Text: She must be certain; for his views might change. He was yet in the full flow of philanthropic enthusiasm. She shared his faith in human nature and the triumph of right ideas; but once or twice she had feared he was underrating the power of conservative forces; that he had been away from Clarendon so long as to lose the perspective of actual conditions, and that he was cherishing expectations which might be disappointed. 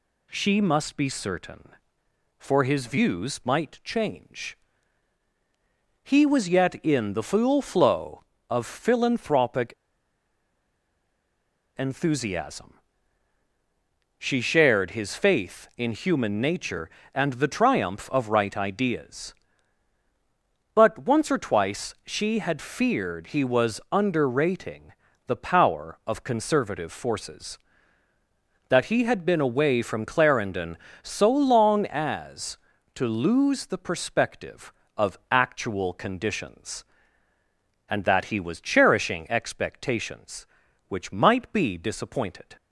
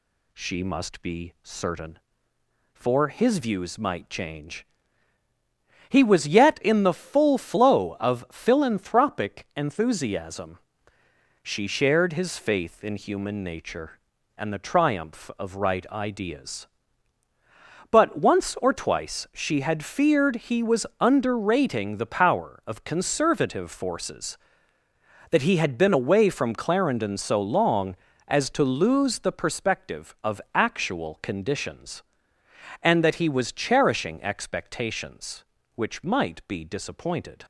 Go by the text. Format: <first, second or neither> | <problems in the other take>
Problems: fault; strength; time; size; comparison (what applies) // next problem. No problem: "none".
second | pauses between "philanthropic" and "enthusiasm"; strong; at 9.7 s; 2.0 s long // pauses between "underrating" and "the"; slight; at 24.9 s; 0.34 s long